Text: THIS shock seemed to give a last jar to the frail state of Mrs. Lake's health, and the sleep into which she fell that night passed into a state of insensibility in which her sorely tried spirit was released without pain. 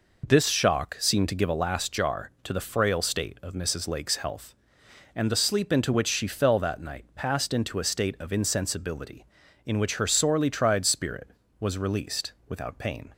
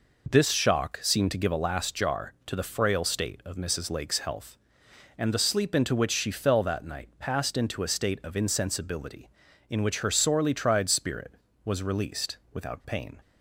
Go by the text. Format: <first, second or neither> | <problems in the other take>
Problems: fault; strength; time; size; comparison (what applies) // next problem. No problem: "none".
neither | none